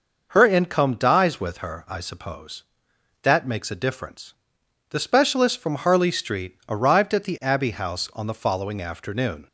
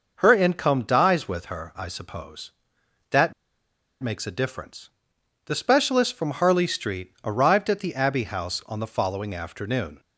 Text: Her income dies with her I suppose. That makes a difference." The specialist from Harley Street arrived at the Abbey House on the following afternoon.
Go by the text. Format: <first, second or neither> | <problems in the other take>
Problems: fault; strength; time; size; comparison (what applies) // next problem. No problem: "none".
first | pauses between "That" and "makes"; noticeable; at 3.3 s; 0.70 s long